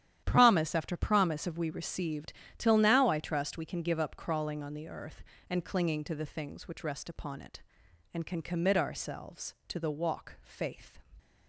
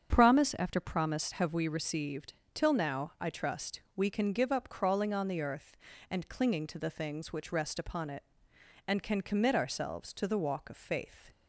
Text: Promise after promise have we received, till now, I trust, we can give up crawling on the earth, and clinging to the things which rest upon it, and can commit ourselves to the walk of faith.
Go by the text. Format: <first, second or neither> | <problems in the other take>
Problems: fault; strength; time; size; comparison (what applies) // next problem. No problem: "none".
second | starts louder than the rest; strong; until 1.2 s; 11 dB; strong in the second // skips "of"; at 10.3 s